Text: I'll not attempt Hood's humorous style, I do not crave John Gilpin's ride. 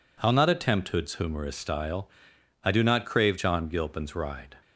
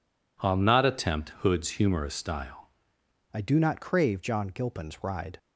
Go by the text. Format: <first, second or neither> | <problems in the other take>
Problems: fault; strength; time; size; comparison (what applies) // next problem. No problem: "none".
first | changes voice at "I"; from 3.3 s on; 2.0 s long